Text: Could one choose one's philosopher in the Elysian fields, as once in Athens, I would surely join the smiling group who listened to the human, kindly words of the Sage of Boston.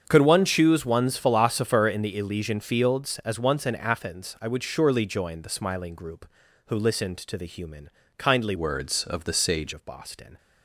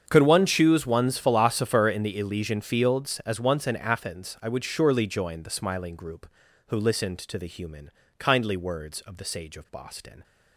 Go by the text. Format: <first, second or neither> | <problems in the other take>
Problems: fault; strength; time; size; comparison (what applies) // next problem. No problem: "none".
second | starts louder than the rest; strong; until 1.0 s; 7.5 dB; strong in the second // changes voice from "words" to "Sage"; from 8.5 to 9.7 s; 1.2 s long